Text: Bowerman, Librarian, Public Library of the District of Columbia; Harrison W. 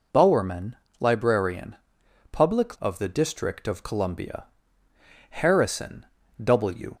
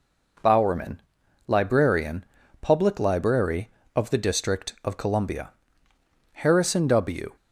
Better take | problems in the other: second | skips "Library"; at 2.7 s // pauses between "Harrison" and "W"; at 6.0 s; 0.38 s long

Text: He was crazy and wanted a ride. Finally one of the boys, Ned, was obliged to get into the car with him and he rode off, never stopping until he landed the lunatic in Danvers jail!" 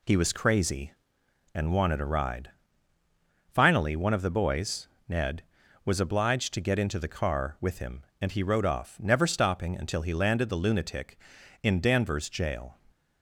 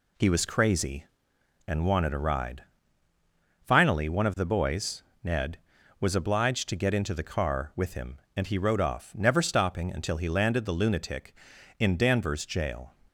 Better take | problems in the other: neither | none

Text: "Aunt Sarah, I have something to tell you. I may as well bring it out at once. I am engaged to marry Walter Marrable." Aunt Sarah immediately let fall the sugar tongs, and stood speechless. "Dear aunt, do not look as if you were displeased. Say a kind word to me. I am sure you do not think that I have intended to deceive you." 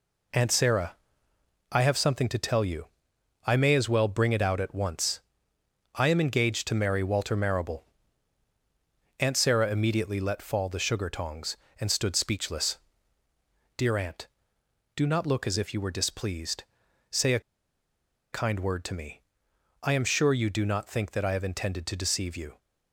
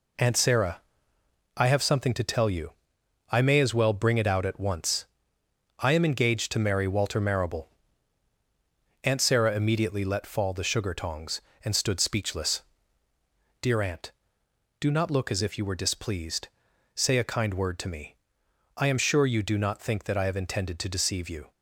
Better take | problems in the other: second | pauses between "a" and "kind"; noticeable; at 17.4 s; 0.92 s long

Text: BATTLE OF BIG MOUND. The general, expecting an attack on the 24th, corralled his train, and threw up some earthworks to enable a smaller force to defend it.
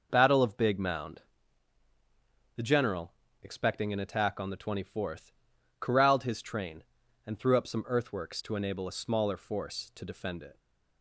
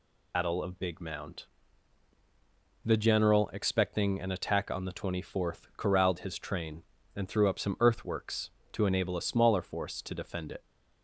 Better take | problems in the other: first | loses the start of "BATTLE"; at 0.3 s; 110 ms

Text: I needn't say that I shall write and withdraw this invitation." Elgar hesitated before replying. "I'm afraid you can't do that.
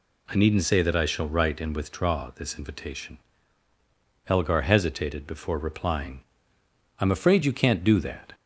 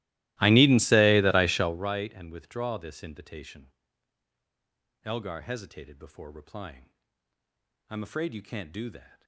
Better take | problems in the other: first | starts louder than the rest; strong; until 1.9 s; 18 dB

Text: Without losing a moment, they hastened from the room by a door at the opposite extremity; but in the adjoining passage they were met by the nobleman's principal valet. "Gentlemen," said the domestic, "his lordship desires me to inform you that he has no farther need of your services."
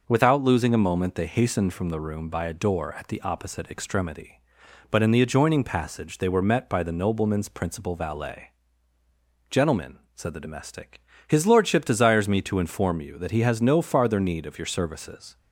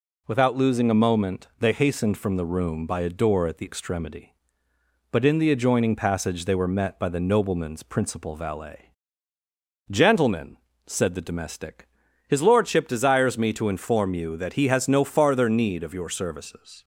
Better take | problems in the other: first | skips "opposite"; at 3.6 s

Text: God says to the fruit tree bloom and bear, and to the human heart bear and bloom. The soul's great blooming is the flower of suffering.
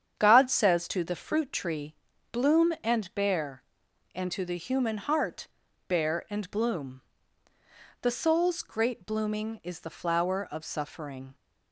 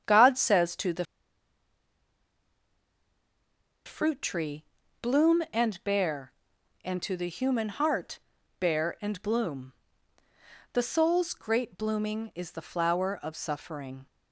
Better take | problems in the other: first | starts louder than the rest; strong; until 3.9 s; 8 dB; strong in the first // pauses between "the" and "fruit"; strong; at 1.0 s; 2.8 s long // pauses between "tree" and "bloom"; at 4.6 s; 0.38 s long; also in the first // pauses between "heart" and "bear"; at 8.1 s; 0.40 s long; also in the first

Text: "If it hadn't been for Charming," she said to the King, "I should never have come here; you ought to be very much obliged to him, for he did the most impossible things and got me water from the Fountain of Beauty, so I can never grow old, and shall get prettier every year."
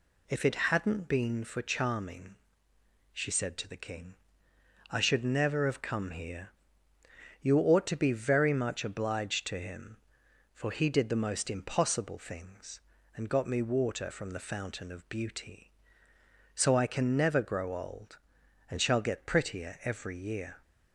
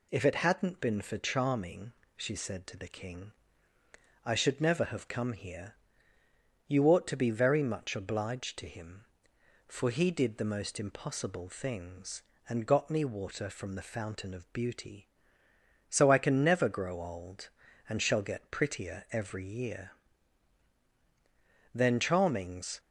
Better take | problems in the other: first | pauses between "prettier" and "every"; slight; at 19.0 s; 0.18 s long // goes on to say "Then Charming's"; noticeable; from 21.7 s on; 1.0 s long

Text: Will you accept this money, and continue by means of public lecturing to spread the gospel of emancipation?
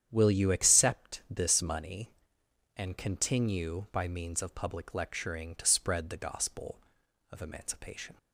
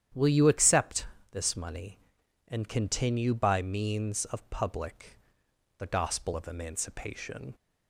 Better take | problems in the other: first | starts louder than the rest; strong; until 1.3 s; 10 dB; strong in the first // pauses between "accept" and "this"; slight; at 1.0 s; 0.24 s long // skips "lecturing to spread"; at 5.4 s

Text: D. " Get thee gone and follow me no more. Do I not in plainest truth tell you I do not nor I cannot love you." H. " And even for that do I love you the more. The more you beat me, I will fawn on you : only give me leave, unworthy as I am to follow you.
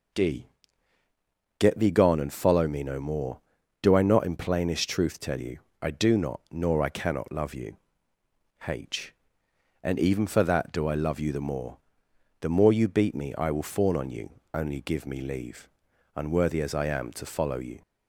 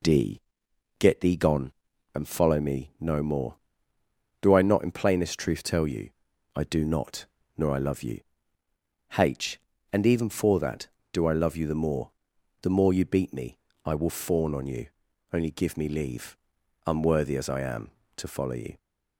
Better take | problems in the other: first | pauses between "you" and "I"; noticeable; at 6.0 s; 0.48 s long; slight in the first // pauses between "not" and "nor"; slight; at 7.2 s; 0.32 s long // skips "cannot"; at 7.7 s

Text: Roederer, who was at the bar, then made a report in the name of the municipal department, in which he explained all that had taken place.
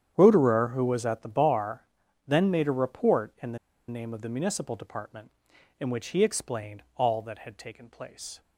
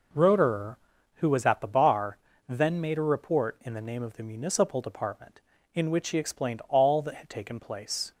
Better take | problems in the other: second | starts louder than the rest; strong; until 1.1 s; 9 dB // pauses between "the" and "name"; slight; at 3.5 s; 0.30 s long

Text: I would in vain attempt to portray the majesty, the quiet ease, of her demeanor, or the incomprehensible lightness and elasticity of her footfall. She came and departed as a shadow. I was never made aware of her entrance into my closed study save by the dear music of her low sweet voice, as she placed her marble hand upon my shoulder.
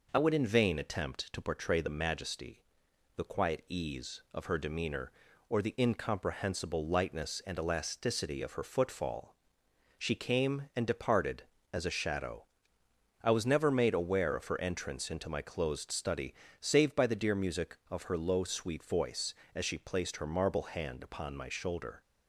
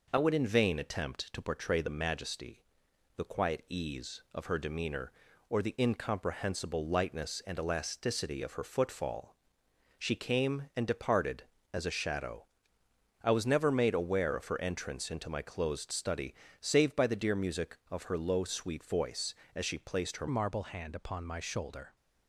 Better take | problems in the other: first | pauses between "study" and "save"; slight; at 16.3 s; 0.26 s long; slight in the first // changes voice at "marble"; from 20.2 s on; 1.7 s long

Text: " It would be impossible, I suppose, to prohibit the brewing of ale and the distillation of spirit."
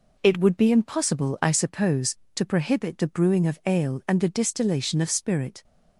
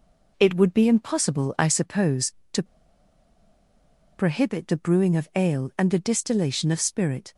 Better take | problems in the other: first | pauses between "to" and "prohibit"; strong; at 2.6 s; 1.5 s long

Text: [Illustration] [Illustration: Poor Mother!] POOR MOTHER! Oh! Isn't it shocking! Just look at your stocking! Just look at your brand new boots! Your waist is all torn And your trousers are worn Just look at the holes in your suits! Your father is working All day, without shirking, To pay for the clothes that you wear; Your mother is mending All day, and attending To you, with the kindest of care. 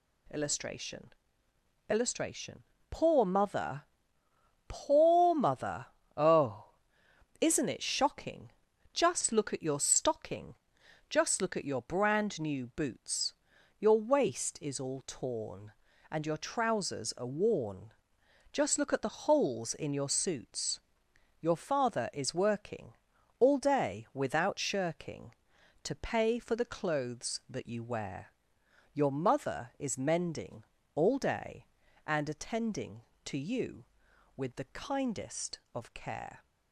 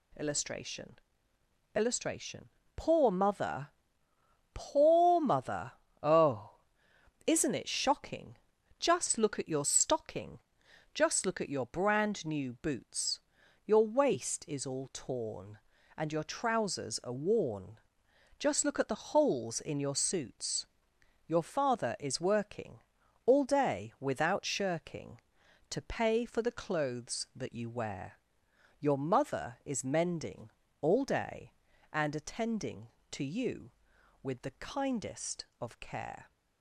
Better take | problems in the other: neither | pauses between "worn" and "Just"; noticeable; the same in both // pauses between "working" and "All"; the same in both // pauses between "mending" and "All"; slight; the same in both

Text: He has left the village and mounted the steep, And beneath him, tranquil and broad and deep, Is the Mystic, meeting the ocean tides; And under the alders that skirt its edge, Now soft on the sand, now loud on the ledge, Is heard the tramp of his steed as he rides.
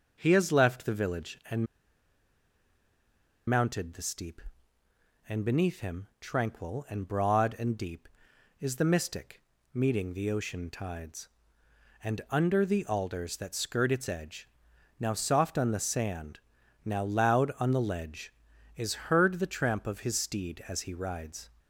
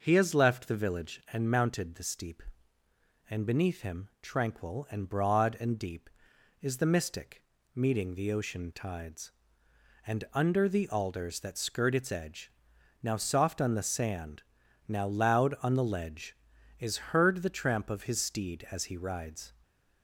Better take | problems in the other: second | pauses between "and" and "mounted"; strong; at 1.6 s; 1.8 s long

